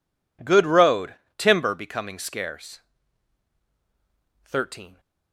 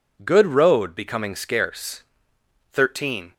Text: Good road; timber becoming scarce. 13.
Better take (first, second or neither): first